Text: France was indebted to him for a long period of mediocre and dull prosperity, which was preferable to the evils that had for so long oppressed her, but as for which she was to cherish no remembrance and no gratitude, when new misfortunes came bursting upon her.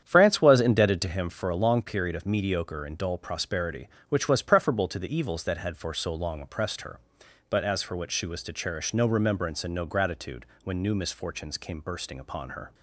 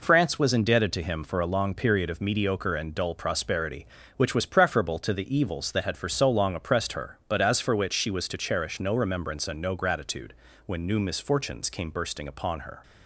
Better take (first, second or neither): second